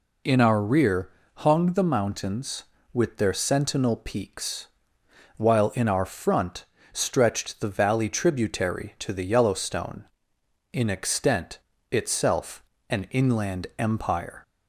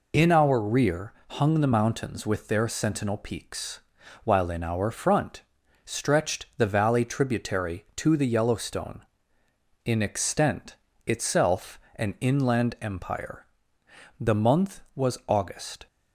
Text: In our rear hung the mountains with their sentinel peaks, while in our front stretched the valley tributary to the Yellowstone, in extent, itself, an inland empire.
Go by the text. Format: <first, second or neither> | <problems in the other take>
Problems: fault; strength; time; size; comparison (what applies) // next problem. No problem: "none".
first | pauses between "rear" and "hung"; slight; at 1.1 s; 0.20 s long; slight in the first // pauses between "front" and "stretched"; at 5.4 s; 0.42 s long; slight in the first // goes on to say "The month was August"; strong; from 14.1 s on; 1.7 s long